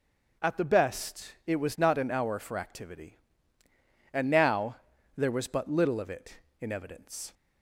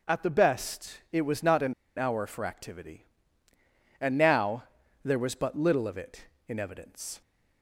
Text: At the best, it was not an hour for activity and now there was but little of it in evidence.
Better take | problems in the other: first | starts louder than the rest; noticeable; until 1.2 s; 6 dB // pauses between "an" and "hour"; slight; at 1.7 s; 0.25 s long // pauses between "now" and "there"; at 4.6 s; 0.40 s long; also in the first

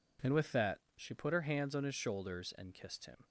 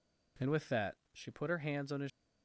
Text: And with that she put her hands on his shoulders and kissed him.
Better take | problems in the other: first | pauses between "that" and "she"; slight; at 0.9 s; 0.18 s long; slight in the first // stops before "shoulders and kissed him"; at 2.0 s

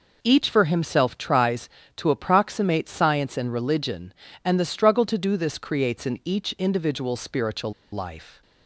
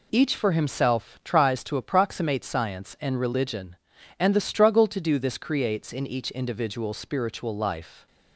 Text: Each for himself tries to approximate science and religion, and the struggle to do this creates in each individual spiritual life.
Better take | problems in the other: second | pauses between "spiritual" and "life"; slight; at 7.7 s; 0.19 s long

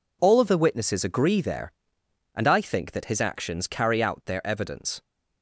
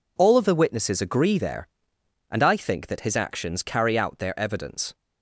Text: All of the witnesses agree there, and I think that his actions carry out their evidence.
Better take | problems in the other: neither | none

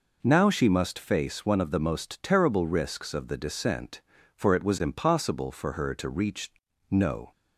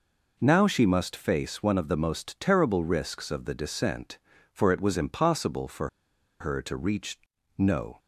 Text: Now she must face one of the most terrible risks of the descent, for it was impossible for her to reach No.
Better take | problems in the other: first | pauses between "for" and "her"; noticeable; at 5.8 s; 0.53 s long // pauses between "reach" and "No"; at 7.1 s; 0.40 s long; also in the first

